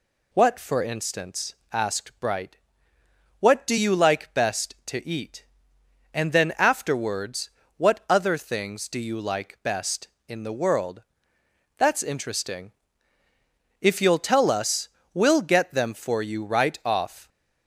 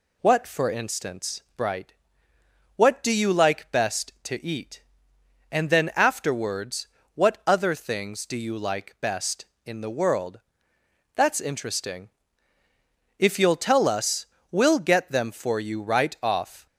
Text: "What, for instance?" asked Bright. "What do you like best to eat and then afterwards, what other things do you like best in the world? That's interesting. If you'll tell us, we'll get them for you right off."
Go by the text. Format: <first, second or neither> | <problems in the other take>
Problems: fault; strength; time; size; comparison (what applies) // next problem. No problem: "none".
first | skips "asked"; at 1.5 s